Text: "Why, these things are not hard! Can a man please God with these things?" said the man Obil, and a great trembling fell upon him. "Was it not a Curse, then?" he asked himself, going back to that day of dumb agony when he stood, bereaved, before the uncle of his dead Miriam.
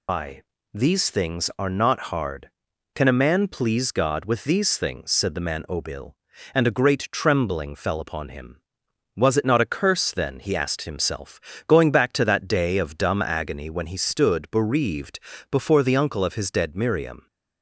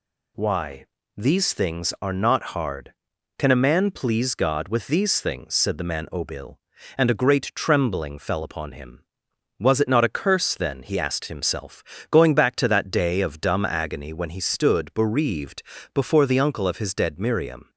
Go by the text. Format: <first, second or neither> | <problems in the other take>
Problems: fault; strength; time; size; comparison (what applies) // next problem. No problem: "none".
second | loses the start of "Why"; at 0.0 s; 165 ms